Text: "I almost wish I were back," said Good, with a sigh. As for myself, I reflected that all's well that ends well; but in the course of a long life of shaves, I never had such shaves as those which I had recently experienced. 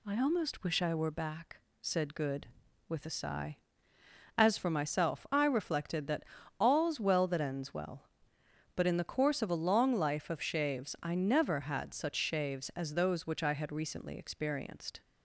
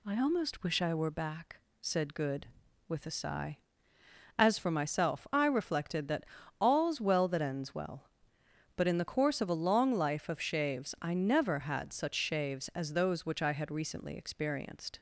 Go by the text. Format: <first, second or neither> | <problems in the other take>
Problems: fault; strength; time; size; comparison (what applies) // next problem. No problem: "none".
neither | pauses between "that" and "all's"; the same in both